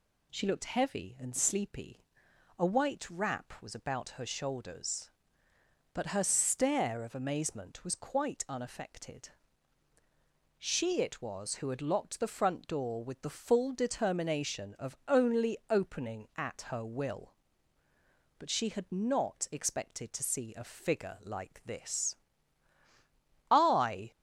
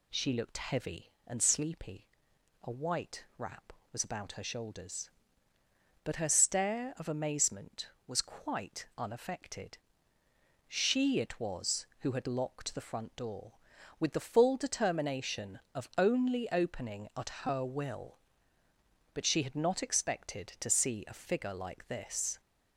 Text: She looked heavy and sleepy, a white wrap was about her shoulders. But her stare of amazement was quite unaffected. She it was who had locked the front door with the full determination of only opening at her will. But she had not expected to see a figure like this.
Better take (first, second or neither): second